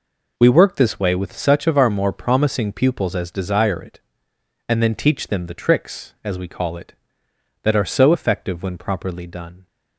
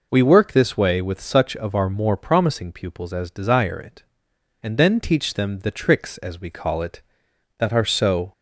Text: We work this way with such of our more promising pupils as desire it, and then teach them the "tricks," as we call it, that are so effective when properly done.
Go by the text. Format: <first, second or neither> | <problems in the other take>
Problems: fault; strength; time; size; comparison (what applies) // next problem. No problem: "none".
first | stops before "effective when properly done"; at 8.3 s